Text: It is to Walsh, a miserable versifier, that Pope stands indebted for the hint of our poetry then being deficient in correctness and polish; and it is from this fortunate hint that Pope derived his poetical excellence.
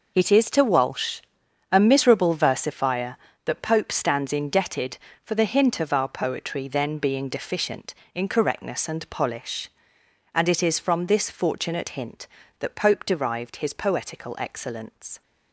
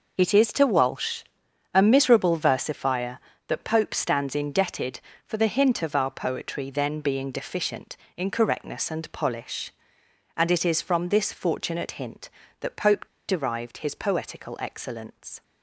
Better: first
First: none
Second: pauses between "Pope" and "derived"; slight; at 13.0 s; 0.22 s long

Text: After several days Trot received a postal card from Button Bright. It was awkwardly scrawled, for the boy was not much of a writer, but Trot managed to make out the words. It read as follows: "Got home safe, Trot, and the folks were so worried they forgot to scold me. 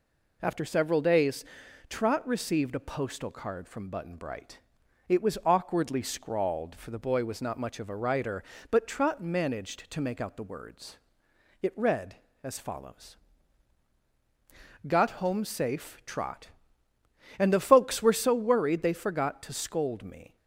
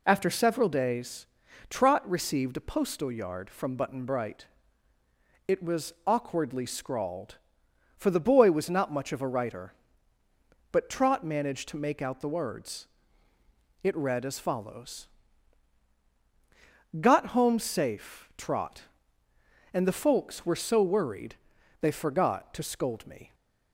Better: first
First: pauses between "days" and "Trot"; at 1.4 s; 0.44 s long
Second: pauses between "days" and "Trot"; at 1.2 s; 0.44 s long // says "yard" for "card"; at 3.0 s // pauses between "worried" and "they"; at 21.3 s; 0.44 s long

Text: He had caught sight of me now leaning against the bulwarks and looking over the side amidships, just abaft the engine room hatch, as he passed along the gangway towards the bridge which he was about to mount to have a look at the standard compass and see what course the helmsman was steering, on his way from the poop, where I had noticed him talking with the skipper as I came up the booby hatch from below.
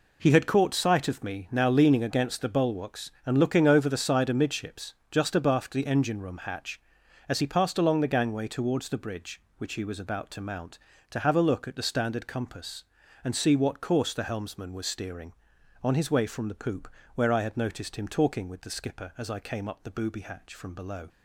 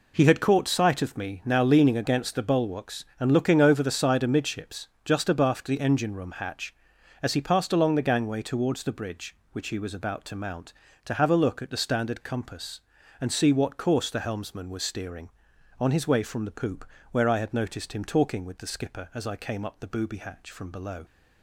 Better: neither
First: none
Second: none

